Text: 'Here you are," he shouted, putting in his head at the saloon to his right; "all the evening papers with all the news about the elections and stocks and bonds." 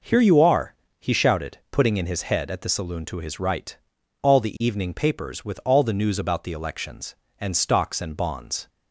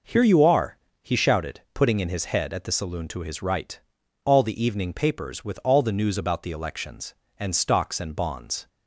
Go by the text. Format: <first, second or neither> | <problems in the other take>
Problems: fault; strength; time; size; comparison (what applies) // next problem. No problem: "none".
neither | none